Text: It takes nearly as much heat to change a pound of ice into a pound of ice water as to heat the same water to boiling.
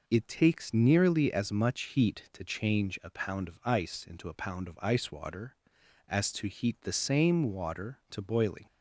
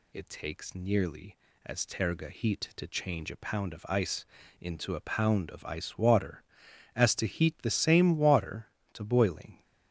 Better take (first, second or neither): first